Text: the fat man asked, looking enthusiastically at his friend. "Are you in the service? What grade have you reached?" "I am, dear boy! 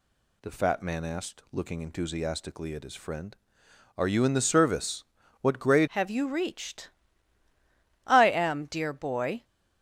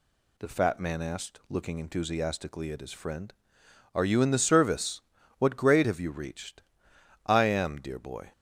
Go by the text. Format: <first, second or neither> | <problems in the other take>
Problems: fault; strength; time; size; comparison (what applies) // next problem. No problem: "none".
second | changes voice at "have"; from 5.8 s on; 3.6 s long